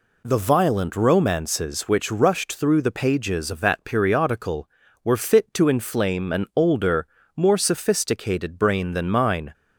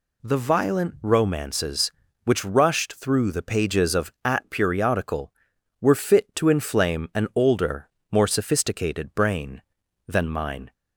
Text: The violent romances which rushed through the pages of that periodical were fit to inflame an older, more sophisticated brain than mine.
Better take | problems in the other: first | says "at" for "that"; at 4.2 s

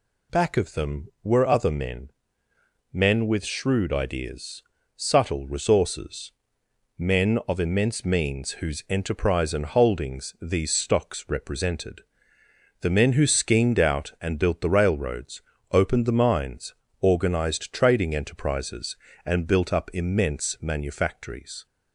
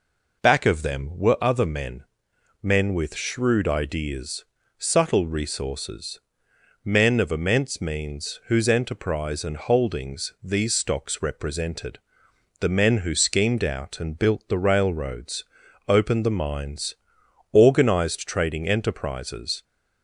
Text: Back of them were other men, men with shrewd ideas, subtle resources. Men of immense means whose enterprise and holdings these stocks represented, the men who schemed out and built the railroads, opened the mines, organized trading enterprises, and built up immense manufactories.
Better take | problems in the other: first | stops before "and built up immense manufactories"; at 19.6 s

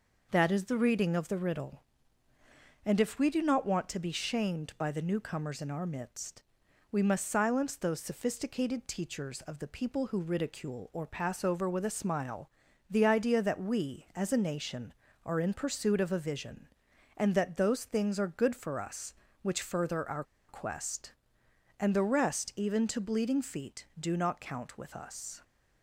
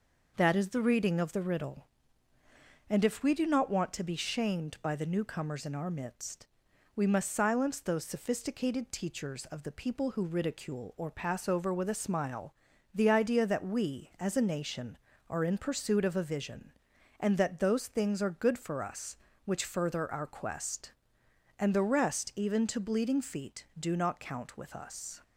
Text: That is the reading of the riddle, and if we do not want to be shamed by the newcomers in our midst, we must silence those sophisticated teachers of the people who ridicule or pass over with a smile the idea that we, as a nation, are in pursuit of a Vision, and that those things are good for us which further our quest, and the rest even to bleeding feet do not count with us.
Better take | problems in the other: second | pauses between "smile" and "the"; at 12.4 s; 0.40 s long; also in the second // pauses between "our" and "quest"; slight; at 20.2 s; 0.24 s long

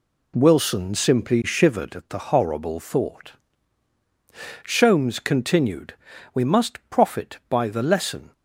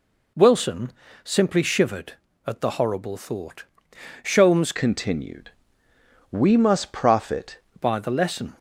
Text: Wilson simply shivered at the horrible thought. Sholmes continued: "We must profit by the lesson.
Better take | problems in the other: first | pauses between "Wilson" and "simply"; slight; at 0.9 s; 0.32 s long // changes voice from "continued" to "profit"; from 4.7 to 7.5 s; 2.8 s long

